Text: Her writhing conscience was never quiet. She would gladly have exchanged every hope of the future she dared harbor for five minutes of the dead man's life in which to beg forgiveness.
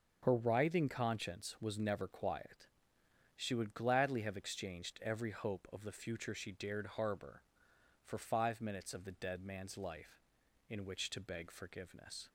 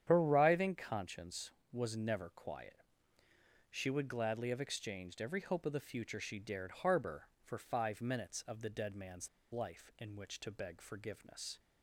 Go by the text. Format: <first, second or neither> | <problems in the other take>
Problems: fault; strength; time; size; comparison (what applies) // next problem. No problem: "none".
first | starts louder than the rest; strong; until 1.0 s; 9 dB; noticeable in the first // pauses between "man's" and "life"; slight; at 9.2 s; 0.23 s long